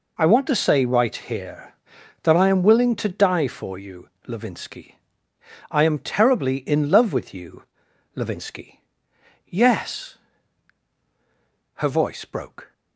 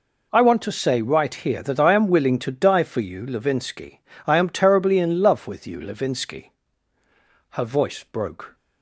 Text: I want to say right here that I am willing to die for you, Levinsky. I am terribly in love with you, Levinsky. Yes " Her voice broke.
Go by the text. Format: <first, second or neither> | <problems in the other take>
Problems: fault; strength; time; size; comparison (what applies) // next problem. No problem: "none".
first | skips "Yes"; at 6.7 s